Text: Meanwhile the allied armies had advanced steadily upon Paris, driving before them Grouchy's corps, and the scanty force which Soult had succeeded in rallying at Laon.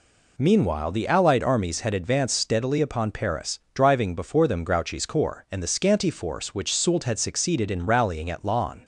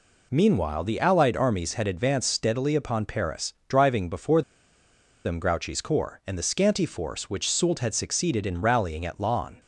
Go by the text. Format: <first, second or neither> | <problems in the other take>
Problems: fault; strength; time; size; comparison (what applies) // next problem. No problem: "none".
first | pauses between "before" and "them"; noticeable; at 4.4 s; 0.82 s long